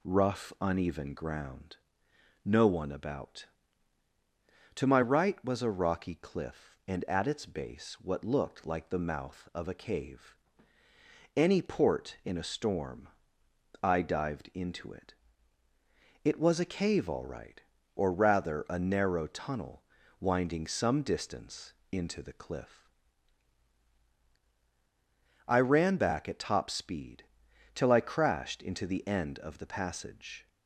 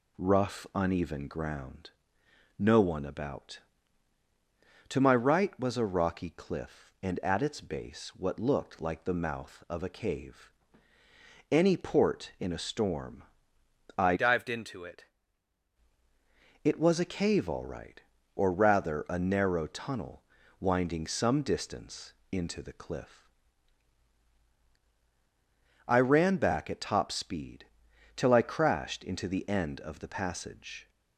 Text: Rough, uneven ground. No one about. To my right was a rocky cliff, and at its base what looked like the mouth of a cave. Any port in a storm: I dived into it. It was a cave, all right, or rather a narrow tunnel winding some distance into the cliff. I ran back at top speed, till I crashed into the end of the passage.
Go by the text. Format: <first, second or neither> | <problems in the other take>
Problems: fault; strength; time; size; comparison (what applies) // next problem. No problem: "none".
first | changes voice from "dived" to "it"; from 14.1 to 15.0 s; 0.9 s long // pauses between "tunnel" and "winding"; slight; at 20.2 s; 0.36 s long; slight in the first // pauses between "distance" and "into"; slight; at 22.1 s; 0.18 s long; slight in the first